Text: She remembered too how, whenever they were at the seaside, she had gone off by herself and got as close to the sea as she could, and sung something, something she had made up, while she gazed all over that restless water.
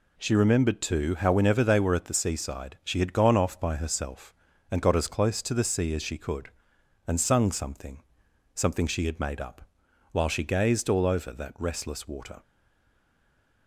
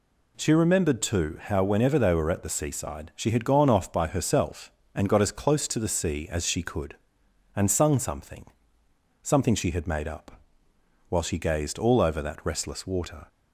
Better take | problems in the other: second | stays silent after the last word; noticeable; from 12.4 s on; 1.2 s long

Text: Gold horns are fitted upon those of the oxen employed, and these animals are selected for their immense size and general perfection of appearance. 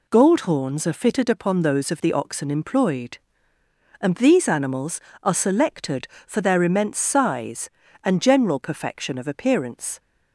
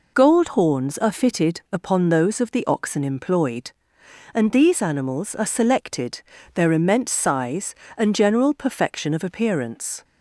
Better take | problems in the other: first | skips "for"; at 6.3 s

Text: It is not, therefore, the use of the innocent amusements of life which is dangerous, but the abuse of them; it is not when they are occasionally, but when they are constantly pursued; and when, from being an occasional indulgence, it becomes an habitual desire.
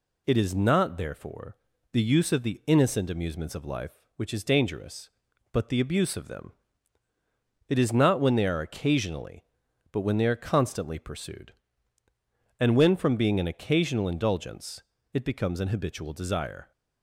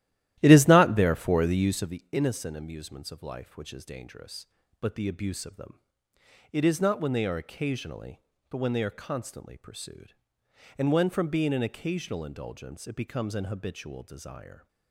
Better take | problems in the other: first | starts louder than the rest; strong; until 1.9 s; 13.5 dB

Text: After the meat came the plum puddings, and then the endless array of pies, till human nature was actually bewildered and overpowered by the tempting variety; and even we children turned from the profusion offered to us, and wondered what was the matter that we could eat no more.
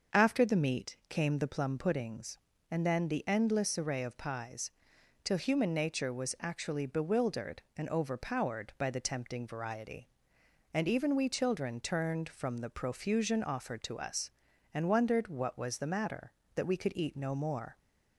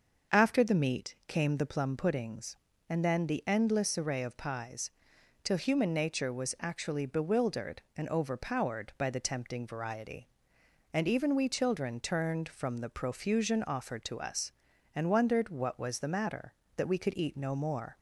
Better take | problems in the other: neither | starts louder than the rest; the same in both

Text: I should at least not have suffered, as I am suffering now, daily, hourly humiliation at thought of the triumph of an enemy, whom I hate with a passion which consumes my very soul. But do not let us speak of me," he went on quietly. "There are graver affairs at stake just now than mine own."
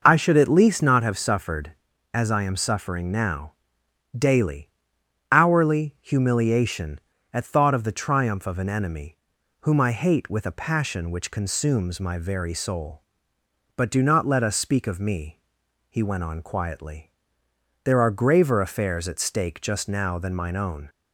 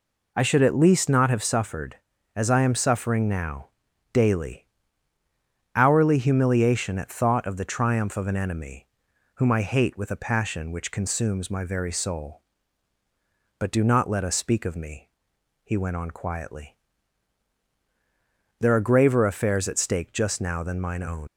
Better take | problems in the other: first | leaves "own" unfinished; at 21.2 s; 100 ms

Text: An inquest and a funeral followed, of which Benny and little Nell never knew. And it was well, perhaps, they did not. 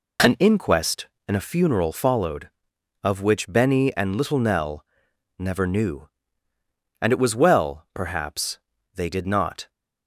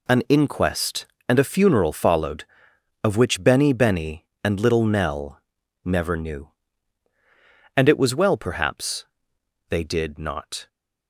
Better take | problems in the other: first | says "Benny" twice; at 3.7 s // pauses between "Nell" and "never"; at 5.3 s; 0.44 s long; noticeable in the first

